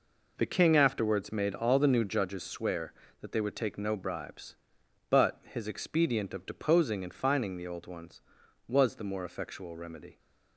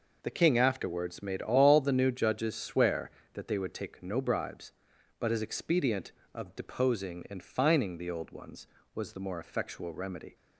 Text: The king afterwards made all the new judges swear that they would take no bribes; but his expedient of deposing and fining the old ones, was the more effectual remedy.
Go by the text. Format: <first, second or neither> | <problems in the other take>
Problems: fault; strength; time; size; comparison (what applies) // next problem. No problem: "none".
neither | none